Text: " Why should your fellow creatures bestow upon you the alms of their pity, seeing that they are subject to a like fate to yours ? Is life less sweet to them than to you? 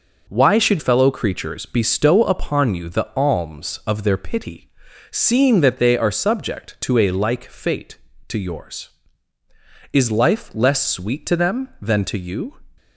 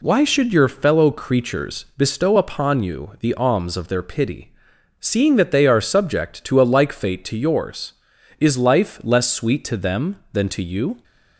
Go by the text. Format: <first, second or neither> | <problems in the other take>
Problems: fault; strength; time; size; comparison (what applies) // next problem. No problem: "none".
second | skips "your"; at 0.7 s